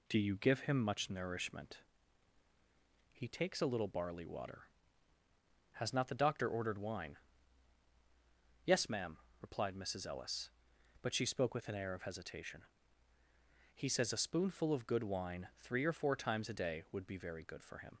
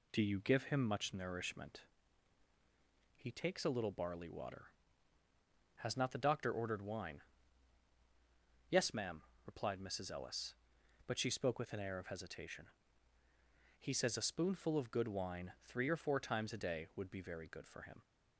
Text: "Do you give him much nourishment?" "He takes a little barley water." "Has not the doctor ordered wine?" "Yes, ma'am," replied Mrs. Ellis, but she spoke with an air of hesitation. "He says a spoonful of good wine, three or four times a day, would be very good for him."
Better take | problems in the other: neither | none

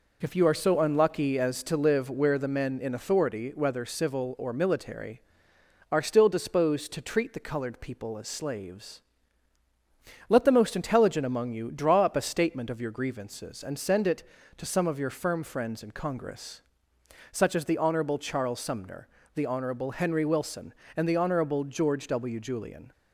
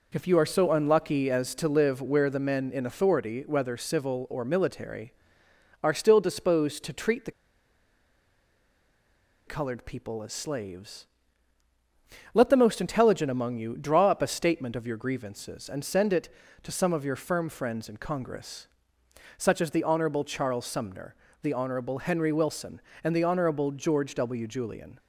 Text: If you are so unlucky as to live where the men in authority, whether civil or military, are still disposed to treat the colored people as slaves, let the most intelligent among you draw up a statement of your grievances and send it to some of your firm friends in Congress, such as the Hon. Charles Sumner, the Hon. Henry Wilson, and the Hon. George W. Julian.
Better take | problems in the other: first | pauses between "the" and "colored"; strong; at 7.3 s; 2.1 s long

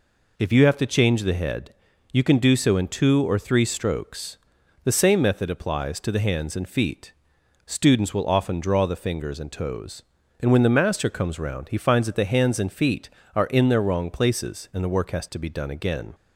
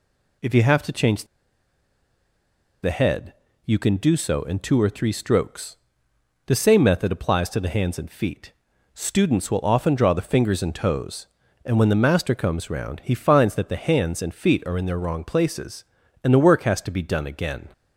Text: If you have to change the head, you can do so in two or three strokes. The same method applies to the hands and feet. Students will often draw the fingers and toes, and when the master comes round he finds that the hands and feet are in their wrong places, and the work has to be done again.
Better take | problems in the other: first | pauses between "change" and "the"; strong; at 1.2 s; 1.5 s long

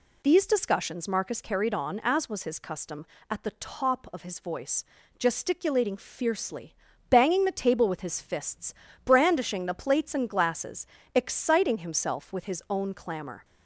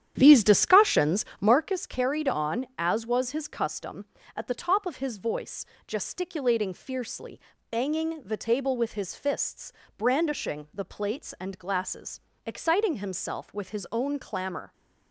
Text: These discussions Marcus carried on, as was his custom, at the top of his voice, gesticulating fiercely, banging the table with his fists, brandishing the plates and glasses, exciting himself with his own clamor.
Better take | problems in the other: first | starts louder than the rest; strong; until 1.7 s; 10 dB

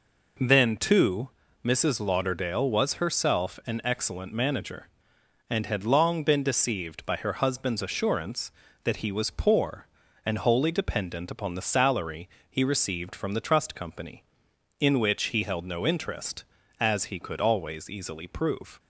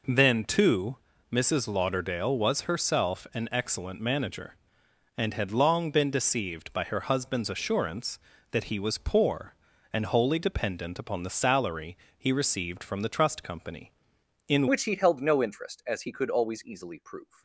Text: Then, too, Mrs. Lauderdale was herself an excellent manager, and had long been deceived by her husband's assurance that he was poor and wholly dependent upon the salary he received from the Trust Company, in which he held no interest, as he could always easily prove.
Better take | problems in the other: first | pauses between "salary" and "he"; slight; at 11.9 s; 0.20 s long; slight in the first // changes voice at "which"; from 14.6 s on; 2.8 s long

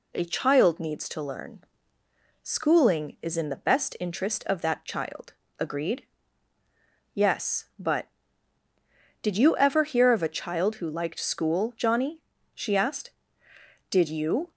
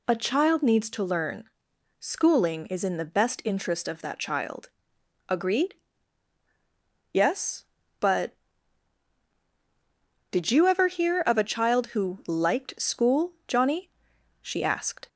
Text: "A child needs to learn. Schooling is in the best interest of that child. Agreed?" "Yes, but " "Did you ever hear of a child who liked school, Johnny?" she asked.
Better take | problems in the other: second | goes on to say "Did you"; noticeable; from 13.8 s on; 0.62 s long

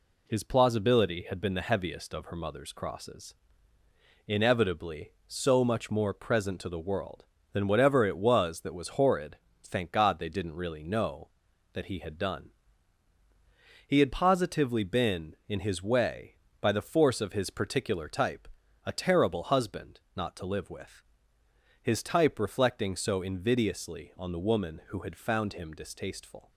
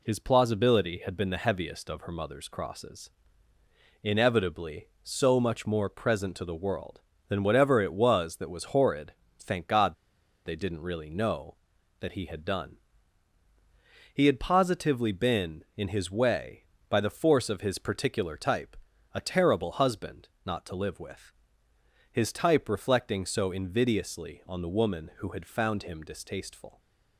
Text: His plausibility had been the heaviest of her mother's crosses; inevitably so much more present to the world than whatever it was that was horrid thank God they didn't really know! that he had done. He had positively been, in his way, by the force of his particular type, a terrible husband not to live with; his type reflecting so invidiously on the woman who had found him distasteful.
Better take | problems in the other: first | pauses between "horrid" and "thank"; slight; at 9.1 s; 0.26 s long; slight in the first // pauses between "God" and "they"; noticeable; at 9.9 s; 0.51 s long // pauses between "husband" and "not"; slight; at 20.2 s; 0.18 s long; slight in the first

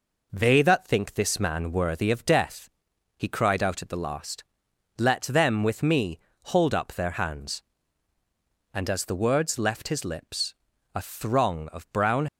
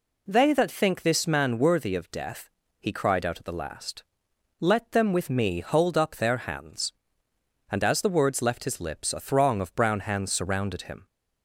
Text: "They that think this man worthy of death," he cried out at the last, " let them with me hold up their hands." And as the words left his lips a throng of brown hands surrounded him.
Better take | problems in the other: second | pauses between "me" and "hold"; slight; at 6.1 s; 0.24 s long // pauses between "lips" and "a"; at 10.5 s; 0.40 s long // stops before "hands surrounded him"; at 12.2 s

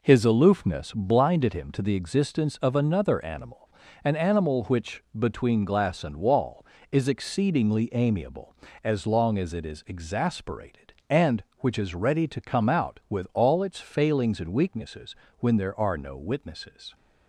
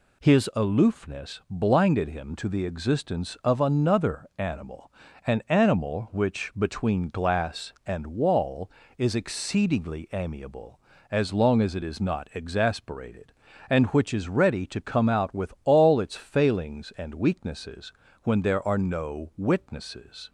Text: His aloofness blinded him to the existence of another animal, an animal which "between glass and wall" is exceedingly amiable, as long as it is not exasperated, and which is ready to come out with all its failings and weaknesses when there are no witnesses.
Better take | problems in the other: second | pauses between "which" and "between"; slight; at 5.0 s; 0.16 s long // skips "not"; at 9.8 s // pauses between "weaknesses" and "when"; slight; at 15.1 s; 0.24 s long; slight in the second

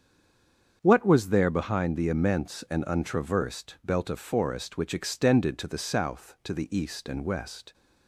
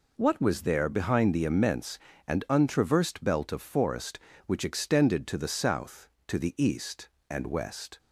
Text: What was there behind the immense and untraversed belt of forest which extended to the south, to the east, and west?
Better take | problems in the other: second | stays silent before the first word; slight; until 0.8 s; 0.8 s long // starts louder than the rest; strong; until 1.8 s; 7.5 dB

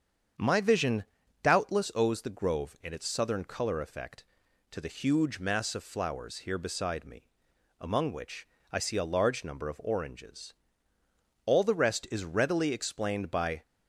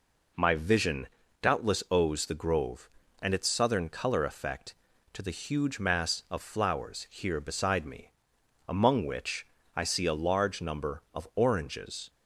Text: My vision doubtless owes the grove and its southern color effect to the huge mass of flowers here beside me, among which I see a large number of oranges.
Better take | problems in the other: second | starts louder than the rest; strong; until 1.7 s; 7.5 dB // pauses between "vision" and "doubtless"; at 1.0 s; 0.38 s long; slight in the second // pauses between "which" and "I"; slight; at 8.4 s; 0.24 s long; slight in the second // goes on to say "All the rest is readily explained by"; strong; from 11.4 s on; 2.1 s long

